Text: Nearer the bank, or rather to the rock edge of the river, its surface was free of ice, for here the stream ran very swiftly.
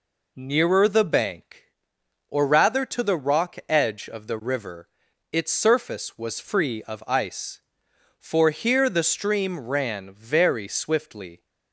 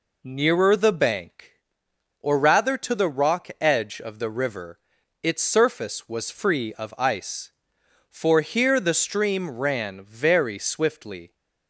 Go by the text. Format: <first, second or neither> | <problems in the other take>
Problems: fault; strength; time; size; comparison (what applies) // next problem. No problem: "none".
neither | none